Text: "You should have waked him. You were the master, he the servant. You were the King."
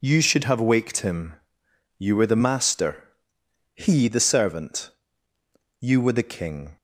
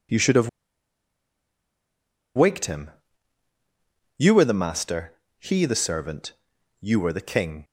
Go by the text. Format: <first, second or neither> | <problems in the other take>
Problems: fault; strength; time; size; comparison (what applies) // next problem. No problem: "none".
first | pauses between "have" and "waked"; strong; at 0.4 s; 1.8 s long